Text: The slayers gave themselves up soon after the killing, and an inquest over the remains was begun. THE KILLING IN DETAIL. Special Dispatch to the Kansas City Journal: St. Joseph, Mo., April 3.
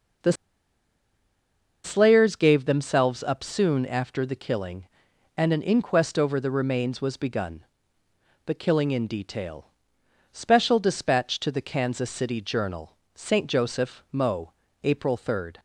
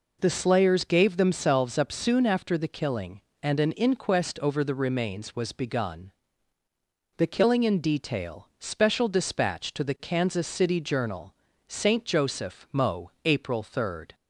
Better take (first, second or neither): second